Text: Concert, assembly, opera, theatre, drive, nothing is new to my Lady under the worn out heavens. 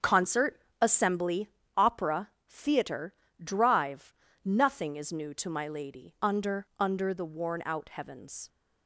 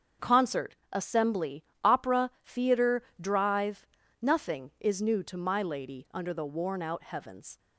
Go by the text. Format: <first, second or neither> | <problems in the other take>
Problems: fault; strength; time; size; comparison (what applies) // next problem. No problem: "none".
second | starts louder than the rest; until 1.2 s; 7 dB; also in the second // says "under" twice; at 6.7 s